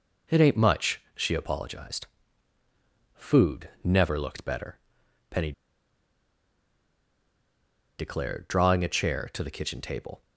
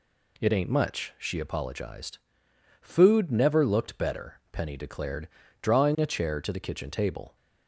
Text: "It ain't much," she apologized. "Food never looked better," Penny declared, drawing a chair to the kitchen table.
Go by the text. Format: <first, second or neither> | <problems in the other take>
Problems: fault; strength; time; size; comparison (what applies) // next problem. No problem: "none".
second | pauses between "Penny" and "declared"; strong; at 5.5 s; 2.4 s long